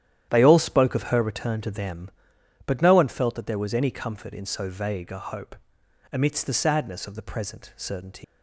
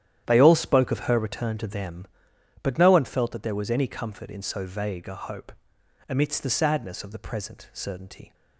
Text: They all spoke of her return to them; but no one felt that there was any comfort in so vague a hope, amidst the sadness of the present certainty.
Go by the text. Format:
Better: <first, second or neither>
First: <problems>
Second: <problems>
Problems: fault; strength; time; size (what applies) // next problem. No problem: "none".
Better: second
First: starts louder than the rest; strong; until 1.3 s; 10.5 dB // leaves "certainty" unfinished; at 8.2 s; 120 ms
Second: starts louder than the rest; strong; until 1.2 s; 10.5 dB